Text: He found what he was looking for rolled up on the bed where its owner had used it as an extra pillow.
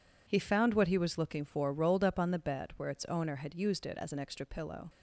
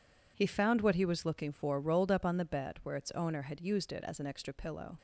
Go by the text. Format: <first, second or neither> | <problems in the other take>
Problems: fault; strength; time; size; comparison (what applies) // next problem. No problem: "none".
neither | none